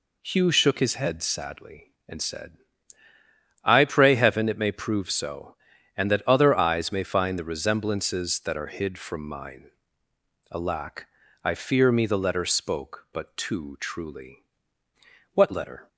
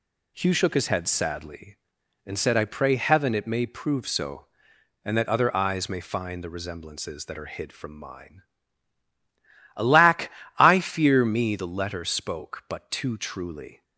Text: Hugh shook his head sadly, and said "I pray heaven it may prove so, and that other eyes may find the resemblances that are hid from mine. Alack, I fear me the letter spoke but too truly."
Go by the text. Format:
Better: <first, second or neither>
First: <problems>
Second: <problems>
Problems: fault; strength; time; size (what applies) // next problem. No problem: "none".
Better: second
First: pauses between "said" and "I"; at 2.5 s; 1.0 s long // goes on to say "What letter"; from 15.3 s on; 0.56 s long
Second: none